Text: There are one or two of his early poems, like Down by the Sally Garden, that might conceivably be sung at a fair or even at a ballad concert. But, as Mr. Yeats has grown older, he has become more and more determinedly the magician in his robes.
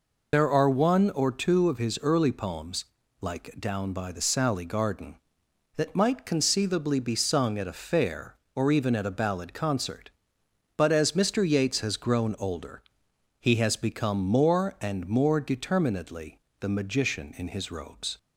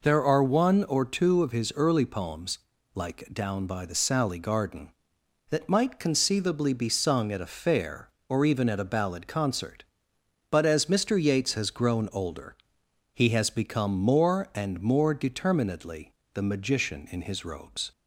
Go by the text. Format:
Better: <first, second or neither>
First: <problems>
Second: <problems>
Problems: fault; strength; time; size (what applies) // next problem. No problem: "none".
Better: second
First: loses the start of "There"; at 0.3 s; 45 ms // pauses between "determinedly" and "the"; slight; at 16.3 s; 0.22 s long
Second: pauses between "determinedly" and "the"; slight; at 16.1 s; 0.22 s long